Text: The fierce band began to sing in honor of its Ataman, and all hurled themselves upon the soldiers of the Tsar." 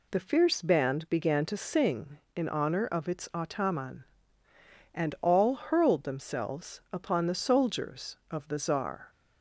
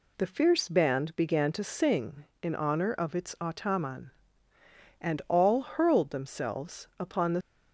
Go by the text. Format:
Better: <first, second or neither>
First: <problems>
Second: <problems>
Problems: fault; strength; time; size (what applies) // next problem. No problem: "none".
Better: first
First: none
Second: stops before "soldiers of the Tsar"; at 7.4 s